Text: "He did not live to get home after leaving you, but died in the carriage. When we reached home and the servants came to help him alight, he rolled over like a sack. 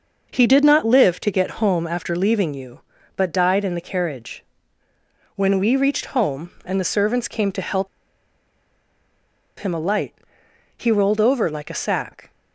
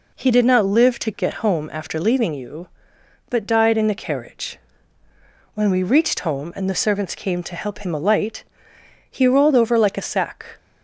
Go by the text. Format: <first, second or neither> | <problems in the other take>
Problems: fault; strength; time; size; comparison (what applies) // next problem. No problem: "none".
second | pauses between "help" and "him"; strong; at 7.8 s; 1.7 s long